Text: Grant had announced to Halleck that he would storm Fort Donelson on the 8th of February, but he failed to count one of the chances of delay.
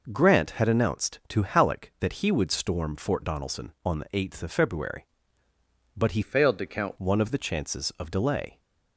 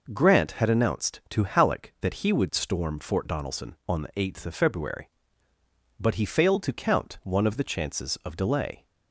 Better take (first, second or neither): second